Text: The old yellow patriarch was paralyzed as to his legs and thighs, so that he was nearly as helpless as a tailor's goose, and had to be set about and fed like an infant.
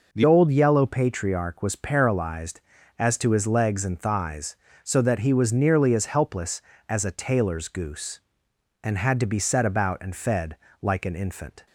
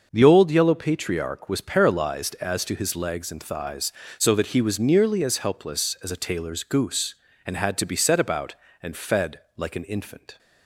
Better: second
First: changes voice at "old"; from 0.2 s on; 11.4 s long // pauses between "fed" and "like"; slight; at 10.5 s; 0.24 s long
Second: pauses between "fed" and "like"; slight; at 9.4 s; 0.18 s long

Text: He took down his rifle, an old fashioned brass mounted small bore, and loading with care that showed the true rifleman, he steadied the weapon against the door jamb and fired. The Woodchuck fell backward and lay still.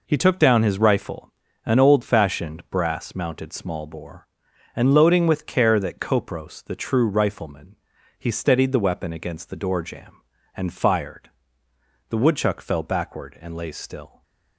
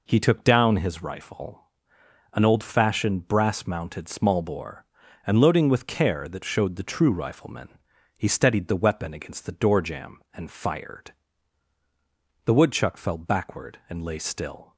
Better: second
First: says "kopros" for "showed"; at 5.9 s // stays silent after the last word; slight; from 14.0 s on; 0.5 s long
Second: none

